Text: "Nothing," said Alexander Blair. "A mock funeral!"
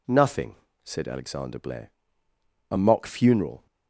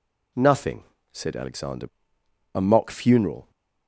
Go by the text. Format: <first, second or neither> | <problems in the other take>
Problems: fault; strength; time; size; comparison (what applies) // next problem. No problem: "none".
first | skips "Blair"; at 2.2 s